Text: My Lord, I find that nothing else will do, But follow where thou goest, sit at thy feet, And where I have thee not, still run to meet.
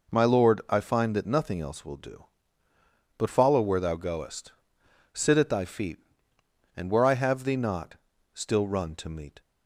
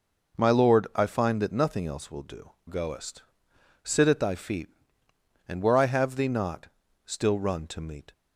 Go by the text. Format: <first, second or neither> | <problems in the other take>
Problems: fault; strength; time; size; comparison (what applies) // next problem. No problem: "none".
first | skips "But follow where thou"; at 2.5 s